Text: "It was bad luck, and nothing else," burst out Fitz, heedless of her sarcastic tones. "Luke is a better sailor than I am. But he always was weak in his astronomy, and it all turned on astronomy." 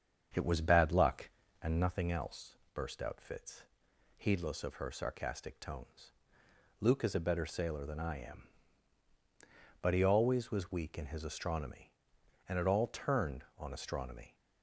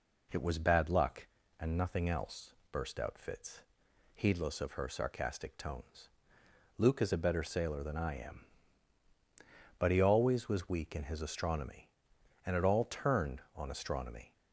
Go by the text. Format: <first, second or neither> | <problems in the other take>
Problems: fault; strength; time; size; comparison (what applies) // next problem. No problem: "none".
second | starts louder than the rest; strong; until 2.1 s; 7.5 dB